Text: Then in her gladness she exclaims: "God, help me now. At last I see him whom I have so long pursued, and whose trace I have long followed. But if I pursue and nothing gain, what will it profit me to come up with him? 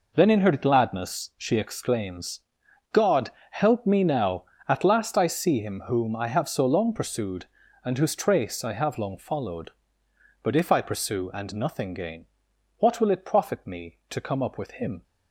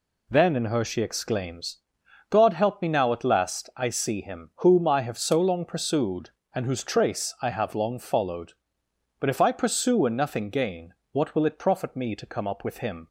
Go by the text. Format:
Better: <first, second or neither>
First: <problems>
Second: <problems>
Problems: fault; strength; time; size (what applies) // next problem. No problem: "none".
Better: first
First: none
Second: skips "gladness"; at 0.8 s